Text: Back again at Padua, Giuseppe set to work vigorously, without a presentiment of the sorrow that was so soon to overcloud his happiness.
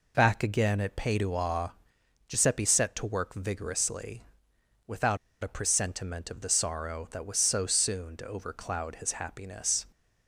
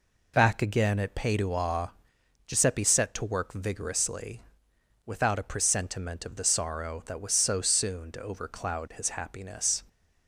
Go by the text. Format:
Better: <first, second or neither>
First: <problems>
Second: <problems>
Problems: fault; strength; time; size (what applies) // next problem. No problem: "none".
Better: second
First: pauses between "without" and "a"; slight; at 5.1 s; 0.26 s long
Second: none